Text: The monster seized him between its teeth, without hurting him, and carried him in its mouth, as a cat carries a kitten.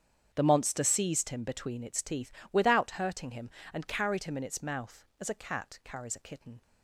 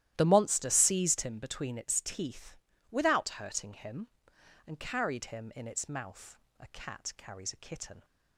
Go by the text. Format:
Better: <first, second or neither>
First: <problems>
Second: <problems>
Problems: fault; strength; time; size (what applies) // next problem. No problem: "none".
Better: first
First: starts louder than the rest; strong; until 1.3 s; 8 dB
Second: starts louder than the rest; strong; until 1.1 s; 13 dB // skips "as"; at 6.4 s